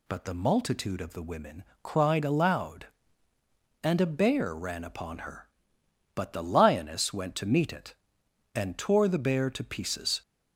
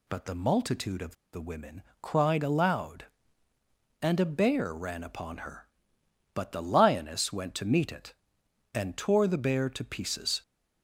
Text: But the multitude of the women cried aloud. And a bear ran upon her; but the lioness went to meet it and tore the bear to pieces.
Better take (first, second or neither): first